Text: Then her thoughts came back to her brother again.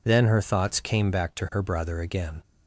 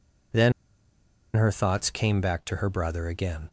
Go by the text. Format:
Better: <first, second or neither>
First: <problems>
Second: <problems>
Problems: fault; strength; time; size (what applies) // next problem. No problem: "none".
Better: first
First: none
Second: pauses between "Then" and "her"; noticeable; at 0.5 s; 0.84 s long